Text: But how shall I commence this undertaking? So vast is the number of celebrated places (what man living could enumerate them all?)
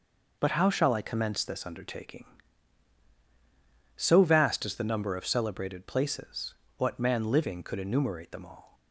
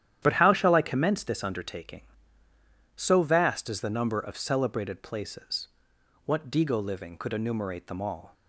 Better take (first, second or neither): first